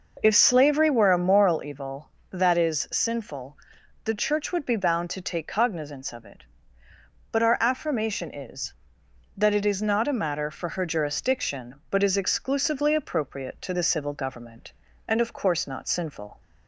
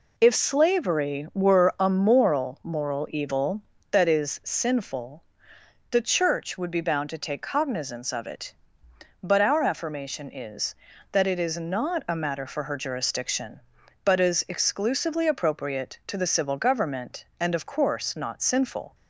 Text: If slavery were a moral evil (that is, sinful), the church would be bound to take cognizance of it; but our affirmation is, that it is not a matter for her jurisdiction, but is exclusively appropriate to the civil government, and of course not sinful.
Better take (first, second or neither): first